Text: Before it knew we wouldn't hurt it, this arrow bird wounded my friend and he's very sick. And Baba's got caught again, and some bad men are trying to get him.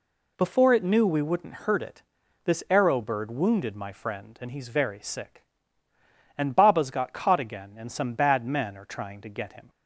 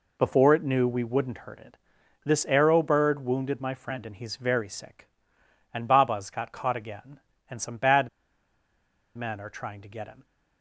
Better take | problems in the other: first | pauses between "bad" and "men"; at 8.0 s; 1.0 s long

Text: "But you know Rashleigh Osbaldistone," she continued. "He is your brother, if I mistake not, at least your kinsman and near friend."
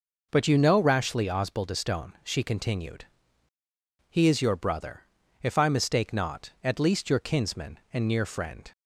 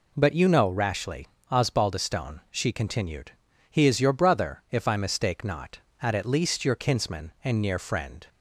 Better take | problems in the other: first | pauses between "Rashleigh" and "Osbaldistone"; slight; at 1.2 s; 0.26 s long // says "at" twice; at 6.1 s

